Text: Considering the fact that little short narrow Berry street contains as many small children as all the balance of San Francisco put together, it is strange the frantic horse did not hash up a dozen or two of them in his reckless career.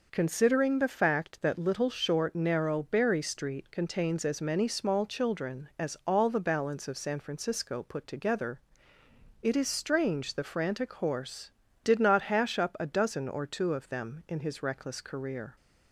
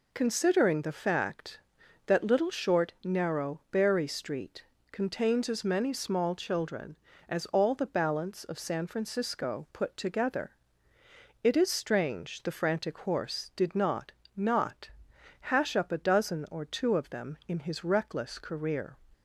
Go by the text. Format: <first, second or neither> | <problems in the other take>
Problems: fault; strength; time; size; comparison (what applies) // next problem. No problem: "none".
first | pauses between "street" and "contains"; slight; at 4.6 s; 0.26 s long // says "not" twice; at 14.3 s